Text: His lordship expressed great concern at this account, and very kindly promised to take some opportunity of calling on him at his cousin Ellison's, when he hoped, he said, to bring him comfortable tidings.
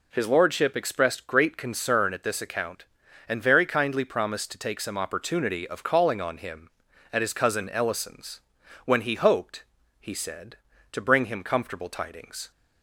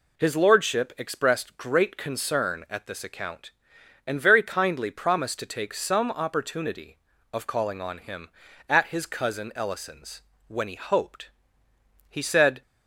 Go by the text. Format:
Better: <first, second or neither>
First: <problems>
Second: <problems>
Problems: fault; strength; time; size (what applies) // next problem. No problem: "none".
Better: first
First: none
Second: stops before "to bring him comfortable tidings"; at 12.6 s